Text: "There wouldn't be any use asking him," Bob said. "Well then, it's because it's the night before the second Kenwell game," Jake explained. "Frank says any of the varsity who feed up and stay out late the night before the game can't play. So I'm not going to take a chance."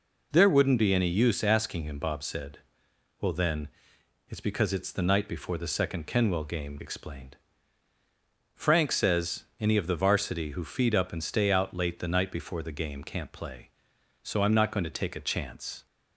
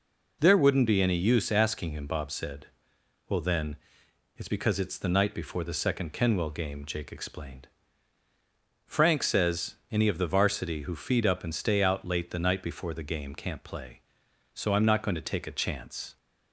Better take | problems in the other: second | skips "Jake"; at 6.7 s

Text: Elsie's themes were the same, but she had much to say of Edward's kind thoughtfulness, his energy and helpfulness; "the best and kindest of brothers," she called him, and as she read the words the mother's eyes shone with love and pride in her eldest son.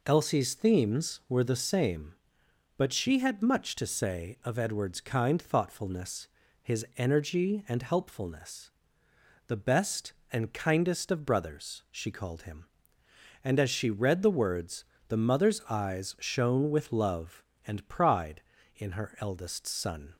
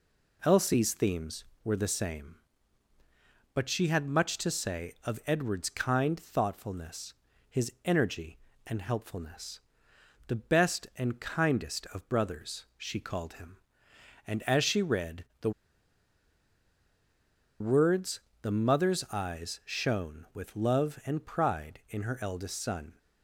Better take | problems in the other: first | pauses between "read" and "the"; slight; at 15.2 s; 0.16 s long // pauses between "the" and "words"; strong; at 15.5 s; 2.0 s long // pauses between "words" and "the"; slight; at 18.2 s; 0.22 s long; slight in the first

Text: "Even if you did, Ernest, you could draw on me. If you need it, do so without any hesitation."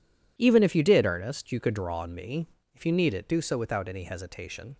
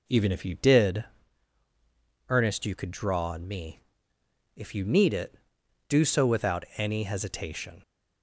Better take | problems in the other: neither | none

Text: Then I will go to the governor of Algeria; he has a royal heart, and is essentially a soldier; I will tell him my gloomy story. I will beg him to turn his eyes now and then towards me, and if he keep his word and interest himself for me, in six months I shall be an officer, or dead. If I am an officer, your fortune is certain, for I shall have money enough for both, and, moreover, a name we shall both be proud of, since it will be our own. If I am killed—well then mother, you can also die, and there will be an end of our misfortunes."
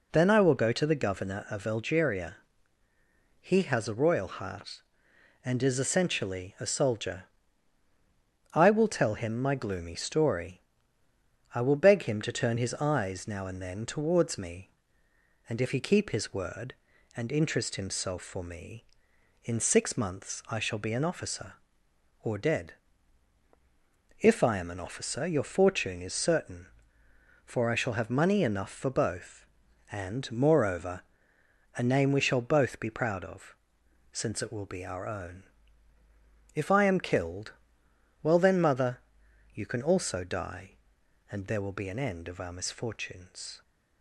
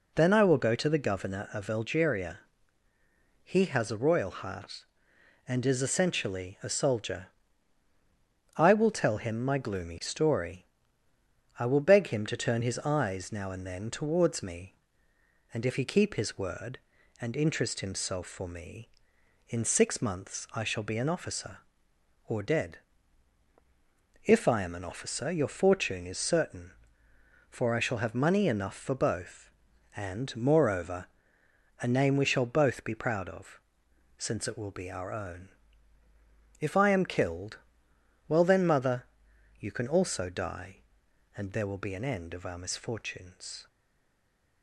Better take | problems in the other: first | stays silent after the last word; from 43.6 s on; 1.0 s long

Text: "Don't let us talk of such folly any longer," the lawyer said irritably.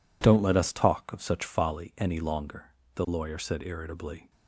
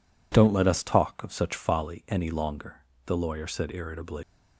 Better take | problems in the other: first | leaves "irritably" unfinished; at 4.2 s; 150 ms

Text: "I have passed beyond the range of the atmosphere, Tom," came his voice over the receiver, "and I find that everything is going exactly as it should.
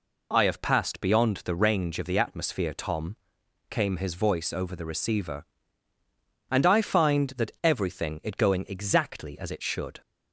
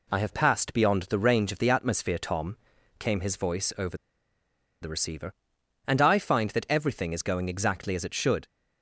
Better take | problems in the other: first | pauses between "over" and "the"; noticeable; at 3.9 s; 0.84 s long

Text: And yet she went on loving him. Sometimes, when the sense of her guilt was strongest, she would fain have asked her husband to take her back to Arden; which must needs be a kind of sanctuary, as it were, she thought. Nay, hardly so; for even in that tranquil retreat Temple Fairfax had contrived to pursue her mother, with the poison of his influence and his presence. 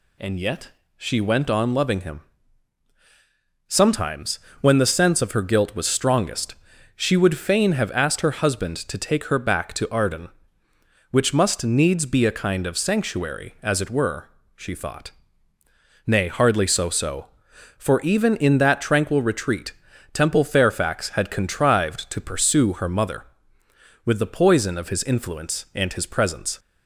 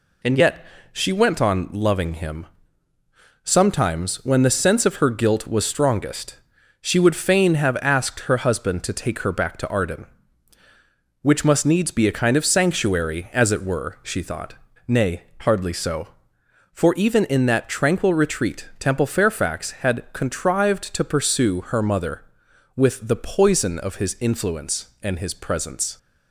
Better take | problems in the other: second | pauses between "yet" and "she"; slight; at 0.6 s; 0.28 s long; slight in the second // says "so" twice; at 16.8 s // pauses between "retreat" and "Temple"; at 19.7 s; 0.40 s long

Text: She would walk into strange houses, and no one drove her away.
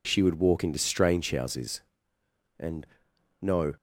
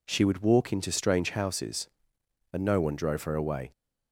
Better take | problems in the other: second | pauses between "and" and "no"; noticeable; at 2.8 s; 0.54 s long // stops before "one drove her away"; at 3.7 s

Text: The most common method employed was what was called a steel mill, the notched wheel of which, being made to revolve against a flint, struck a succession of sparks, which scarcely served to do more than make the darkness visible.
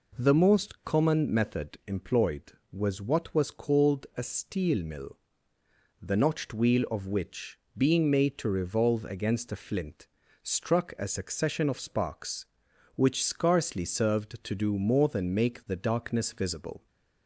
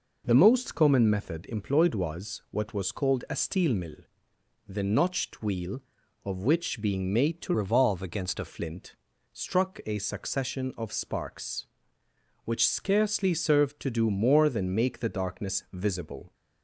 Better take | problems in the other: first | changes voice from "revolve" to "a"; from 7.5 to 8.4 s; 0.9 s long

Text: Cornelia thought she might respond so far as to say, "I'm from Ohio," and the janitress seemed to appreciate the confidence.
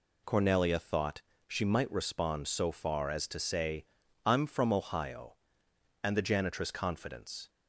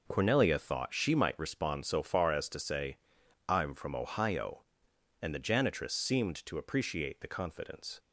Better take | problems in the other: second | pauses between "thought" and "she"; slight; at 1.2 s; 0.26 s long // skips "seemed to appreciate the"; at 6.6 s

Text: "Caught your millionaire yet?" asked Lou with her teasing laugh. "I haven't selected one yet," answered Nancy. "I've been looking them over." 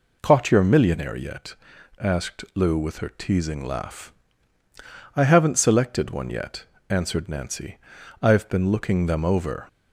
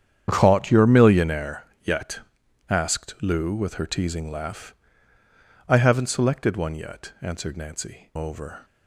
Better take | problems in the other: first | starts louder than the rest; strong; until 1.2 s; 9 dB // pauses between "millionaire" and "yet"; slight; at 1.6 s; 0.18 s long // skips "I've been looking them"; at 8.1 s

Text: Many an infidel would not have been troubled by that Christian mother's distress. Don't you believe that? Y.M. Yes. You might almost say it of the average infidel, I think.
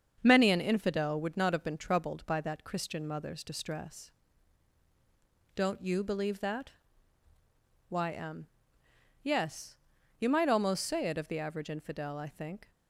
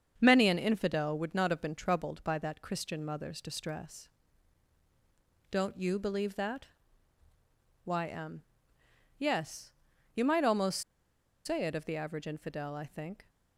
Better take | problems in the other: first | starts louder than the rest; strong; until 1.2 s; 7 dB; strong in the first // pauses between "almost" and "say"; noticeable; at 10.8 s; 0.64 s long

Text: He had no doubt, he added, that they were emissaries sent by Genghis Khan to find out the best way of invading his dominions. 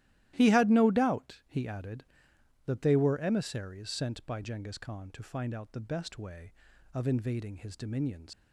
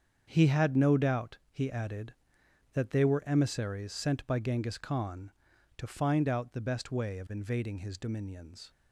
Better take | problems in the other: second | starts louder than the rest; strong; until 1.3 s; 14.5 dB; strong in the second // leaves "dominions" unfinished; at 8.3 s; 125 ms

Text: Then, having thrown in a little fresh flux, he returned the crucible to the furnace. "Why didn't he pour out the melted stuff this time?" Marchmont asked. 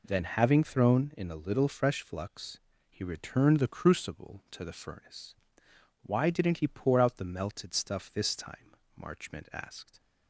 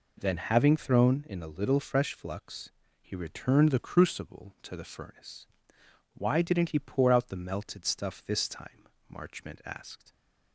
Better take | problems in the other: neither | none

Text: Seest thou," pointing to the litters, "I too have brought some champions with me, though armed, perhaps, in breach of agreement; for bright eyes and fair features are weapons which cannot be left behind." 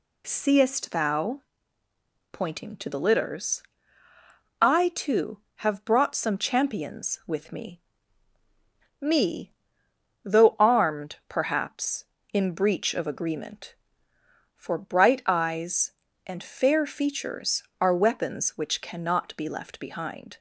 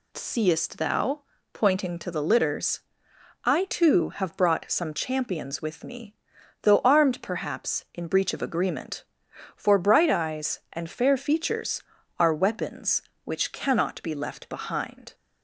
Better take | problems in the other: second | says "me" twice; at 8.9 s

